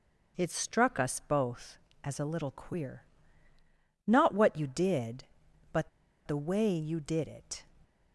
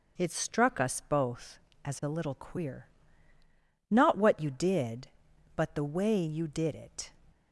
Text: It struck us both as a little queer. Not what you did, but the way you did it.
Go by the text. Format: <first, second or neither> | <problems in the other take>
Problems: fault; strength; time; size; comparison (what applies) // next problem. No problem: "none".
second | pauses between "but" and "the"; at 5.8 s; 0.37 s long